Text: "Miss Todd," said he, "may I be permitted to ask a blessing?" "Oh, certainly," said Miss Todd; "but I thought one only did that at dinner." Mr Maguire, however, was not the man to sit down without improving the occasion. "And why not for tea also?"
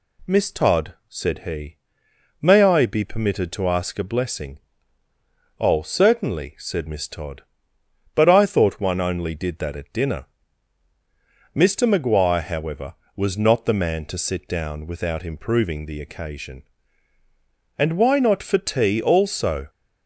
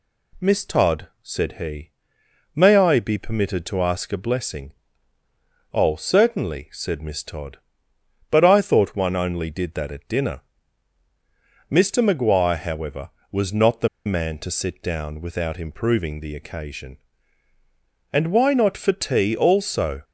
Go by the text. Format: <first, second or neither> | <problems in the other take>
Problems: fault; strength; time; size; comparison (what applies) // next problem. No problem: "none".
first | pauses between "the" and "man"; slight; at 13.8 s; 0.17 s long